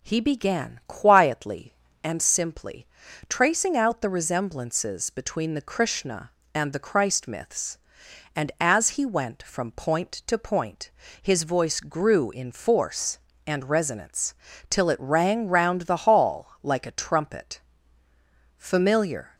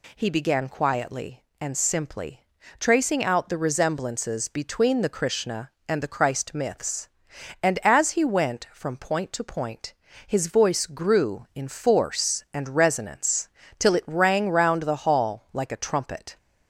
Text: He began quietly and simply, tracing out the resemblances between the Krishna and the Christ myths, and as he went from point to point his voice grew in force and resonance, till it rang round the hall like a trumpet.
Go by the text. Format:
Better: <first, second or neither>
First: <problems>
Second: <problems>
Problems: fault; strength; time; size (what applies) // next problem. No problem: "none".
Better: second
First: pauses between "point" and "his"; slight; at 10.8 s; 0.32 s long // goes on to say "Familiar"; noticeable; from 18.5 s on; 0.78 s long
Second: pauses between "point" and "his"; slight; at 9.9 s; 0.34 s long